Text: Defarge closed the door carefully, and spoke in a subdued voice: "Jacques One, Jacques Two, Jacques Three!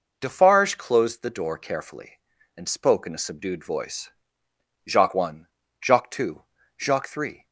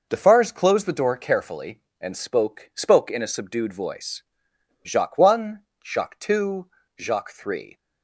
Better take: first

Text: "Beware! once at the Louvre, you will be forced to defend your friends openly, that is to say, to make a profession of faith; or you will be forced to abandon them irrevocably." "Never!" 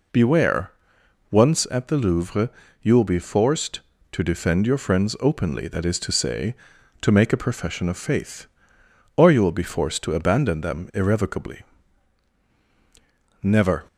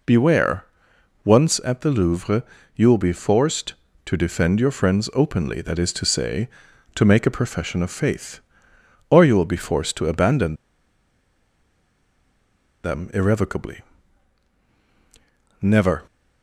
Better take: first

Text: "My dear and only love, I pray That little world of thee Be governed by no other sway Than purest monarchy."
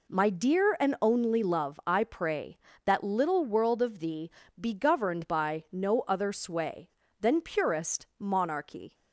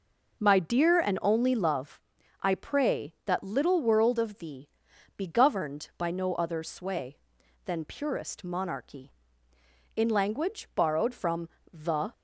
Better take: first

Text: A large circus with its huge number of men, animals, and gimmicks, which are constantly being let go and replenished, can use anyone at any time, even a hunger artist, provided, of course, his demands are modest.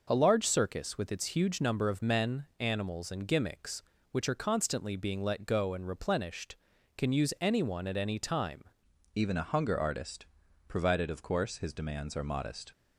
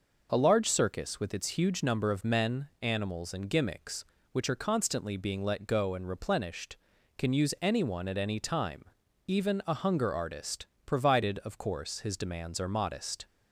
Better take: second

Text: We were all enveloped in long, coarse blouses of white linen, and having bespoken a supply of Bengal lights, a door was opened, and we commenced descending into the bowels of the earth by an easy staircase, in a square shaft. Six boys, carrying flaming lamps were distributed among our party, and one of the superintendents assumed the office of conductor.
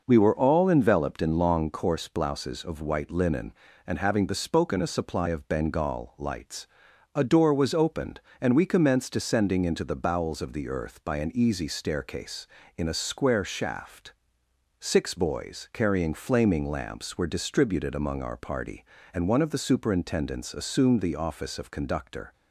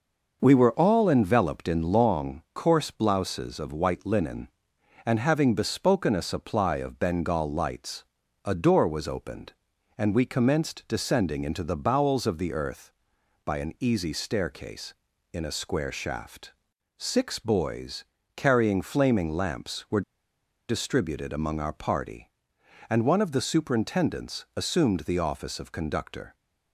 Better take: first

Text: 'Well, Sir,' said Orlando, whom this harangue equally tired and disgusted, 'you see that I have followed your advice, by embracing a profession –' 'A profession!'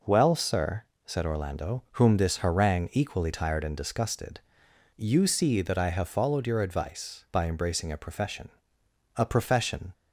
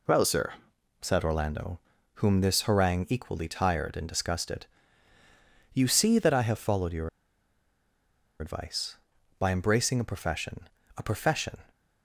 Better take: first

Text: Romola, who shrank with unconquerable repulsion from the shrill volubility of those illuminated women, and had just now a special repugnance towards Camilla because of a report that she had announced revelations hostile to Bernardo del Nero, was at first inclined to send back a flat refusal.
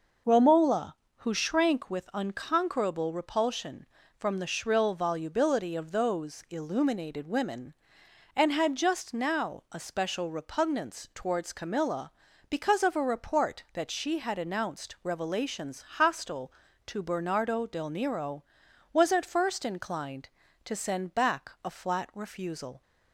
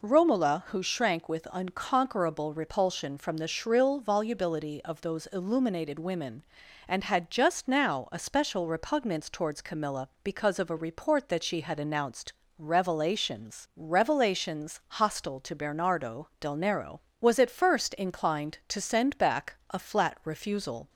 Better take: first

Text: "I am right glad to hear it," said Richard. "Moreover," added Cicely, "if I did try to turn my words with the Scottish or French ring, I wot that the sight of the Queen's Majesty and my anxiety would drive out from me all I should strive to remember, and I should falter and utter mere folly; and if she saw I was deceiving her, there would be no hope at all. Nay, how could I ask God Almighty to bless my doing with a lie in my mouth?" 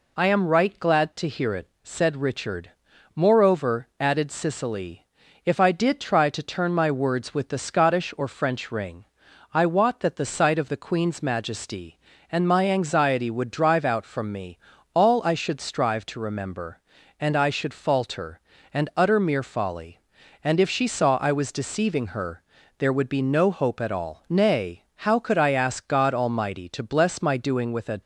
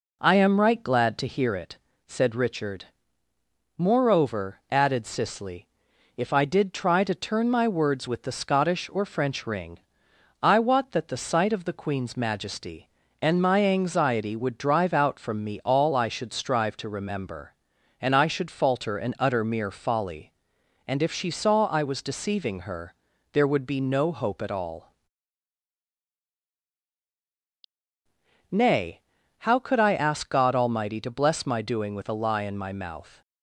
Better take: second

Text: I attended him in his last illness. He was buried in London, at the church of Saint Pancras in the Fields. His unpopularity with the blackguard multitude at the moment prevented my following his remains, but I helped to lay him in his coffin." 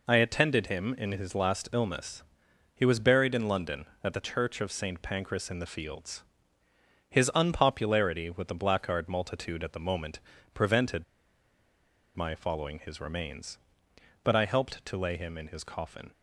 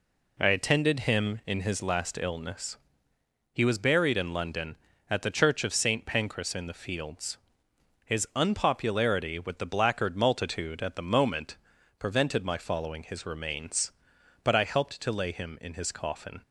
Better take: second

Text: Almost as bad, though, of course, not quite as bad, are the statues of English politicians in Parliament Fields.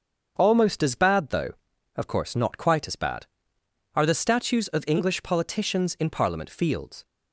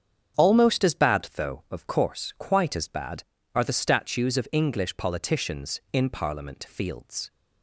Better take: first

